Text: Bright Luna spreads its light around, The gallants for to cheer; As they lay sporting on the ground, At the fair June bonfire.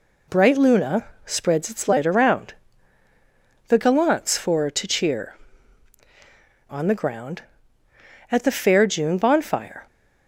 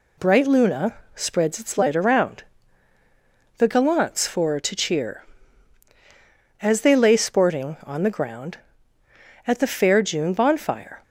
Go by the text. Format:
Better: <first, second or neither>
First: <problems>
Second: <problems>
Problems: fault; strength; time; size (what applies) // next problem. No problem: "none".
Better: second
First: pauses between "Luna" and "spreads"; slight; at 1.0 s; 0.18 s long // skips "As they lay sporting"; at 6.0 s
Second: pauses between "Luna" and "spreads"; slight; at 0.9 s; 0.18 s long